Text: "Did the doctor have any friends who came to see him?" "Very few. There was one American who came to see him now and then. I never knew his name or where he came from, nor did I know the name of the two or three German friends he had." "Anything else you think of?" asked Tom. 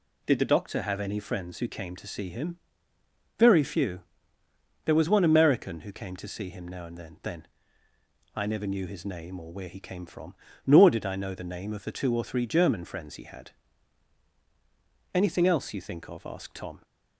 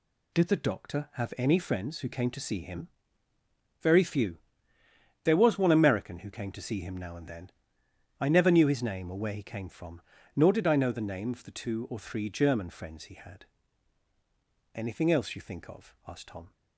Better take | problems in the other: second | says "then" twice; at 7.2 s

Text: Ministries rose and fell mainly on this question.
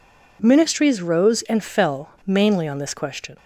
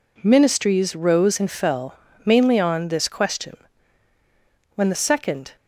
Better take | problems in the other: first | pauses between "fell" and "mainly"; slight; at 1.9 s; 0.28 s long // goes on to say "When the second"; noticeable; from 4.7 s on; 0.80 s long

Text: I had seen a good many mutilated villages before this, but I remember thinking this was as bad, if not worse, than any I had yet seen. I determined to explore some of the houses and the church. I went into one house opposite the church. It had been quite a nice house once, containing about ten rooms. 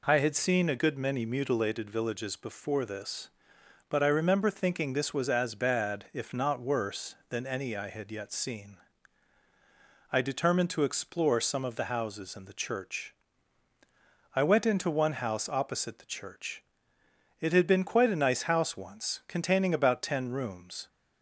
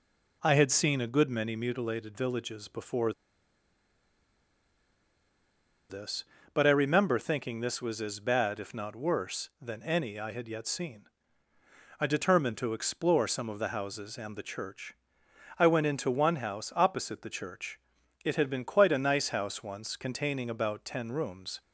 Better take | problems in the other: first | pauses between "before" and "this"; strong; at 3.1 s; 2.7 s long

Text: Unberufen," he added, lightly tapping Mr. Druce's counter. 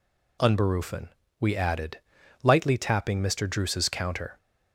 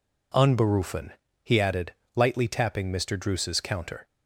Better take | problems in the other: second | says "we" for "he"; at 1.3 s

